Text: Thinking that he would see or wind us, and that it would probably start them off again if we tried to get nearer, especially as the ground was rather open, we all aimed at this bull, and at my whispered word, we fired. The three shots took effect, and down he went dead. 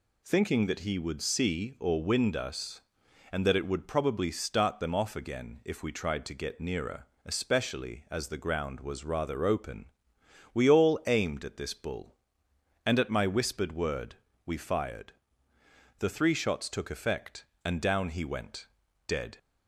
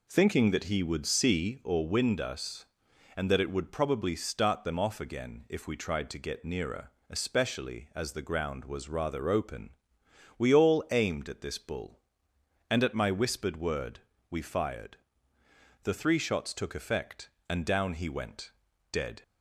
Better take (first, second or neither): first